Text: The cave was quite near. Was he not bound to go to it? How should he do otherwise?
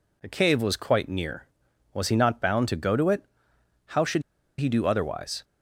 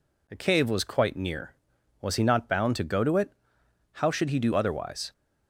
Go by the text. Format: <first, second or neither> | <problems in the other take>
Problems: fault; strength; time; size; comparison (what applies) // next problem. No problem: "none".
second | pauses between "should" and "he"; at 4.2 s; 0.37 s long